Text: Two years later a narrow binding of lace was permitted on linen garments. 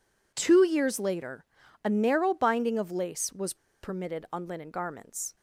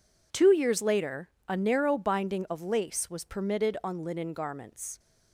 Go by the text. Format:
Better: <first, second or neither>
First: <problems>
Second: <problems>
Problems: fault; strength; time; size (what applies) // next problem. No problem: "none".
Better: second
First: pauses between "later" and "a"; at 1.4 s; 0.38 s long // pauses between "was" and "permitted"; slight; at 3.5 s; 0.27 s long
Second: pauses between "later" and "a"; slight; at 1.2 s; 0.20 s long